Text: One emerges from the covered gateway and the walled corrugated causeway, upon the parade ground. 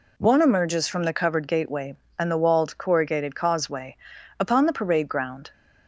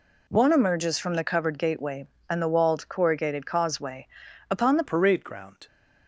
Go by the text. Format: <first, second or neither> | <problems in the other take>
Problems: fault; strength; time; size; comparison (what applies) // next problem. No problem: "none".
first | changes voice at "parade"; from 4.8 s on; 0.8 s long